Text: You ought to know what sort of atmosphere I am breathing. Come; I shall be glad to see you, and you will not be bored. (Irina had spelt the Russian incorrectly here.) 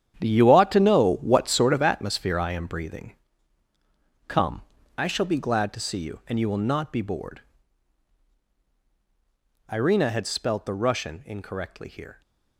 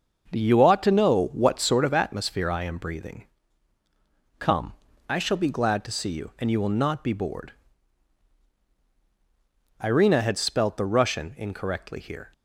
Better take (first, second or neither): second